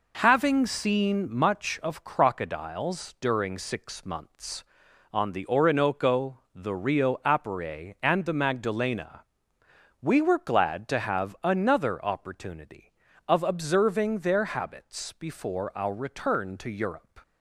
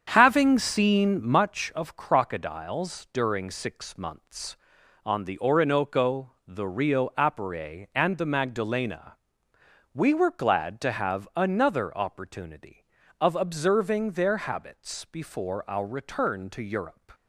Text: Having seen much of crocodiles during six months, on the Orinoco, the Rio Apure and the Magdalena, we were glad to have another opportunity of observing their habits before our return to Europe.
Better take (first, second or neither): first